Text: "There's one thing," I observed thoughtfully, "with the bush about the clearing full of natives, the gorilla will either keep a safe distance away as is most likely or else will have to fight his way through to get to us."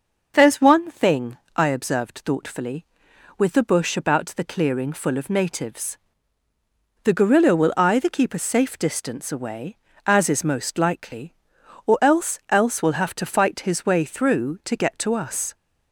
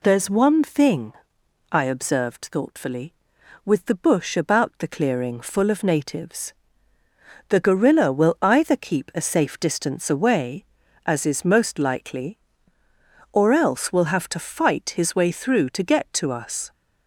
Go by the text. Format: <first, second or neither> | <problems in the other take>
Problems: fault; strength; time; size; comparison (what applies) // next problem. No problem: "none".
second | says "else" twice; at 12.4 s